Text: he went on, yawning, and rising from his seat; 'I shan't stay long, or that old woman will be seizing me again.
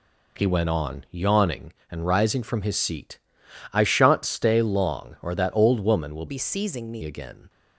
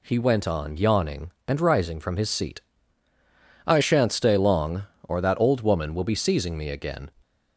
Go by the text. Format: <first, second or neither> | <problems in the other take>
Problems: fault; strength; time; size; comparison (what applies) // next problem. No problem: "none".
second | changes voice from "be" to "me"; from 6.2 to 7.0 s; 0.8 s long